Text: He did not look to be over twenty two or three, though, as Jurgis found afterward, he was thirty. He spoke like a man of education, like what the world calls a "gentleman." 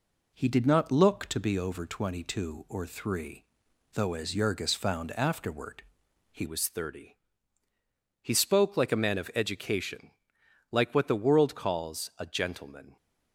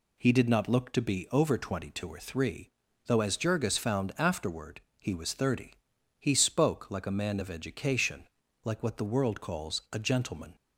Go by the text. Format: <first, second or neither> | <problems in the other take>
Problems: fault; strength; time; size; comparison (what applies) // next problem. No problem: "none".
second | changes voice at "was"; from 6.4 s on; 6.5 s long